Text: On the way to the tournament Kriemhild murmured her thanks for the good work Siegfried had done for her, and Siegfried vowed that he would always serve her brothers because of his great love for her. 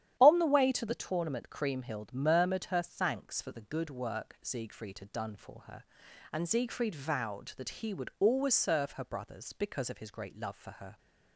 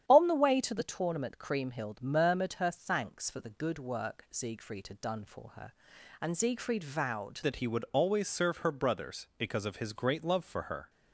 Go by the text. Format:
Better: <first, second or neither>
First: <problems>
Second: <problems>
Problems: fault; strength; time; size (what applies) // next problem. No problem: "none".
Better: first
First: starts louder than the rest; strong; until 1.2 s; 10.5 dB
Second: starts louder than the rest; strong; until 1.0 s; 10 dB // changes voice at "that"; from 7.4 s on; 3.4 s long